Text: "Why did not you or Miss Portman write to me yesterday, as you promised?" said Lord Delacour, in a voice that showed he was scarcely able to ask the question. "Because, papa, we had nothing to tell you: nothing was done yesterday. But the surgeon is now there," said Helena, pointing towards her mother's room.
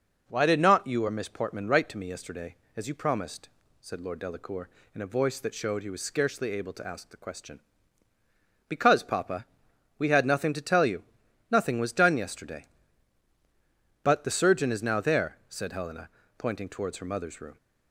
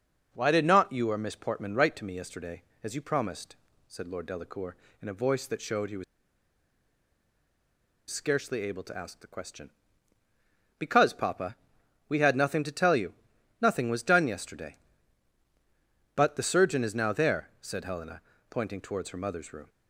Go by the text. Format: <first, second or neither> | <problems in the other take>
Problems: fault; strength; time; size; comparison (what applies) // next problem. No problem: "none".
first | pauses between "was" and "scarcely"; strong; at 6.0 s; 2.0 s long